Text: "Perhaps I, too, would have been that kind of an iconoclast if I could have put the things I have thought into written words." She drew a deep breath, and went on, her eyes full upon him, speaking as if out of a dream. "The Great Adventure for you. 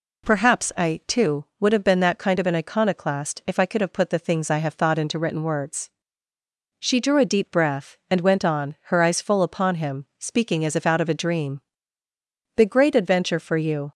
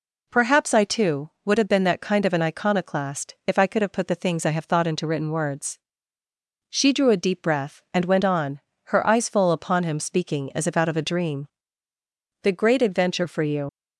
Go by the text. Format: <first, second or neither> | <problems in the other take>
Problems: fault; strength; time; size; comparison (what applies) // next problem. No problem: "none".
first | leaves "you" unfinished; at 13.6 s; 70 ms